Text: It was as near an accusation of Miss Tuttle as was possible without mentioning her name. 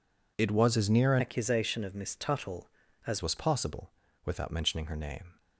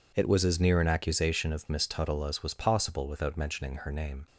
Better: second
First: changes voice from "accusation" to "as"; from 1.1 to 3.2 s; 2.1 s long // pauses between "possible" and "without"; slight; at 3.9 s; 0.32 s long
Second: none

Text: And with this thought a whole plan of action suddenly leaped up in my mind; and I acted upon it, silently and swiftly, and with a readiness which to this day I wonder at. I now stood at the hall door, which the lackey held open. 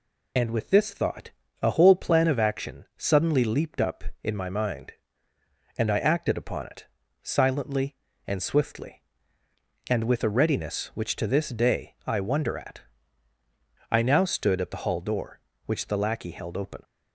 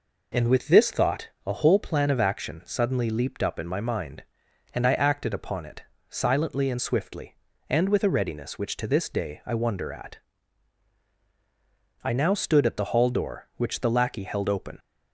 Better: second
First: loses the start of "And"; at 0.3 s; 40 ms // pauses between "thought" and "a"; slight; at 1.3 s; 0.30 s long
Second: pauses between "thought" and "a"; slight; at 1.2 s; 0.16 s long

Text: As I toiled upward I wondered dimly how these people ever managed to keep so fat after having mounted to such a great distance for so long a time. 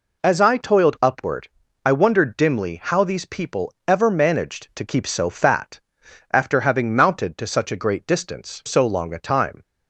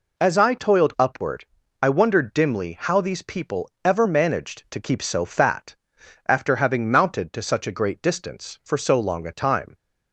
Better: second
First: pauses between "upward" and "I"; at 1.4 s; 0.38 s long // pauses between "people" and "ever"; slight; at 3.7 s; 0.16 s long // pauses between "fat" and "after"; noticeable; at 5.7 s; 0.54 s long // skips "for"; at 8.6 s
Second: pauses between "upward" and "I"; at 1.4 s; 0.38 s long // pauses between "people" and "ever"; slight; at 3.6 s; 0.16 s long // pauses between "fat" and "after"; noticeable; at 5.7 s; 0.54 s long

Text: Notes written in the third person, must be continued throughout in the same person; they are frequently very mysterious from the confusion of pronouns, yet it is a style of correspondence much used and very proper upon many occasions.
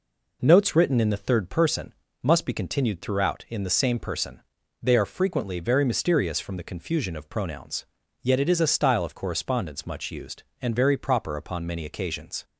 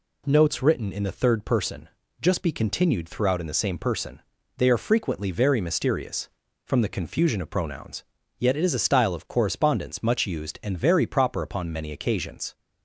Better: first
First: none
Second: says "just" for "must"; at 2.1 s

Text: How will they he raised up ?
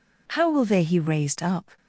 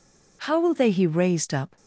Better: neither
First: none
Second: none

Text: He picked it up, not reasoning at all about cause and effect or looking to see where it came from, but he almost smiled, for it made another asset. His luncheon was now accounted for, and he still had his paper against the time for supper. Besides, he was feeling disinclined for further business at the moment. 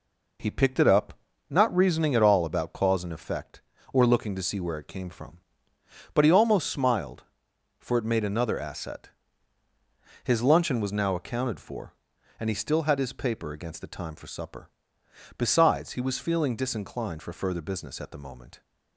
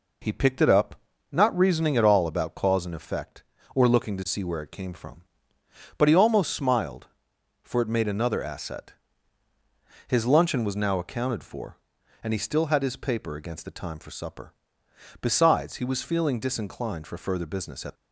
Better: first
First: none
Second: stops before "the moment"; at 17.9 s

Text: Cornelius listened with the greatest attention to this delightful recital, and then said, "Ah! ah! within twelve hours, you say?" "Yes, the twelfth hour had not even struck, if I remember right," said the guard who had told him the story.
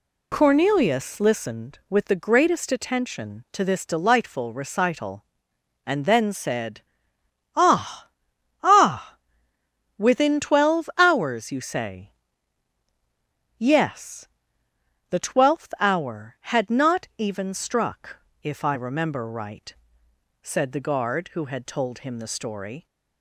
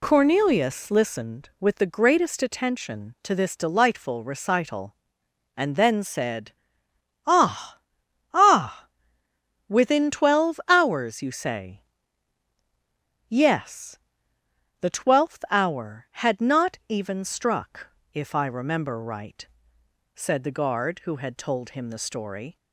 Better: neither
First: none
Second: none

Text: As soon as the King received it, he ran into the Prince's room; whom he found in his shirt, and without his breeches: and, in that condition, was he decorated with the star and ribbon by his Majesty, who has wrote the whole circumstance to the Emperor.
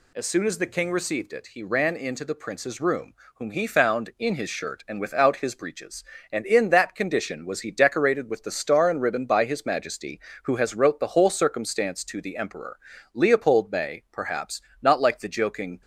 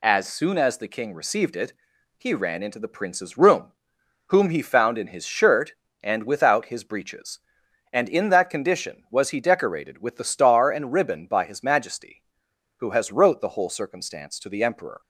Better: second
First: goes on to say "Leopold may perhaps not like the joking"; strong; from 13.1 s on; 2.6 s long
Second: none

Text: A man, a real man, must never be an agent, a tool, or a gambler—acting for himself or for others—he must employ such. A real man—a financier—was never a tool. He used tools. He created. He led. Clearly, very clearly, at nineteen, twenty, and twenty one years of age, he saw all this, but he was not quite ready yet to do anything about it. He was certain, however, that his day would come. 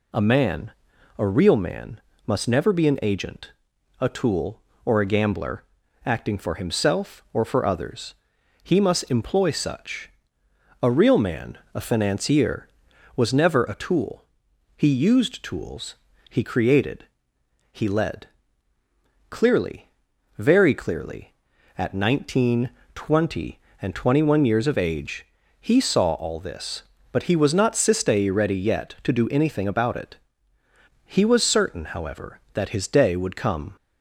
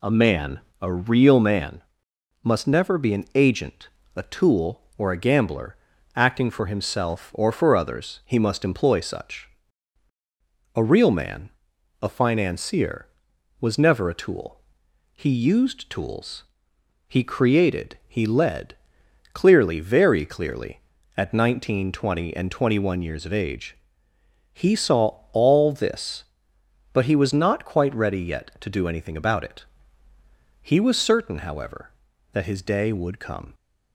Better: second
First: says "sistei" for "quite"; at 27.7 s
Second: none

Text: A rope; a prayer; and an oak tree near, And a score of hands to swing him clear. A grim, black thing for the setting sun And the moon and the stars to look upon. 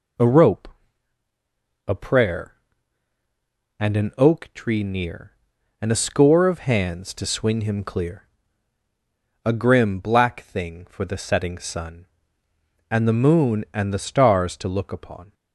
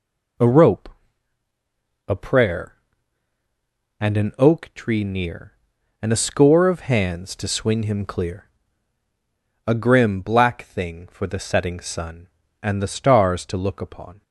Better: first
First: none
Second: skips "And the moon"; at 12.4 s

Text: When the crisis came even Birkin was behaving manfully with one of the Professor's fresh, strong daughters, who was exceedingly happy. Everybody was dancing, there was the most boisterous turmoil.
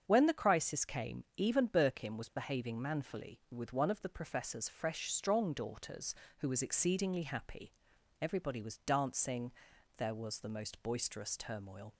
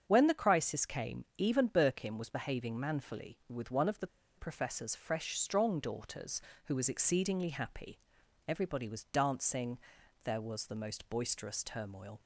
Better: first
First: starts louder than the rest; strong; until 1.0 s; 7.5 dB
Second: starts louder than the rest; strong; until 1.0 s; 7.5 dB // pauses between "the" and "Professor's"; slight; at 4.0 s; 0.31 s long

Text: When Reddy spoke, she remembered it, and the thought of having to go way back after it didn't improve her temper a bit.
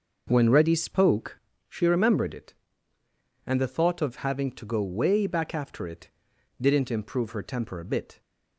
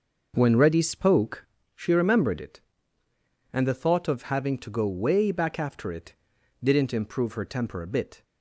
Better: neither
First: pauses between "it" and "didn't"; noticeable; at 6.1 s; 0.50 s long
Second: pauses between "it" and "didn't"; noticeable; at 6.1 s; 0.48 s long

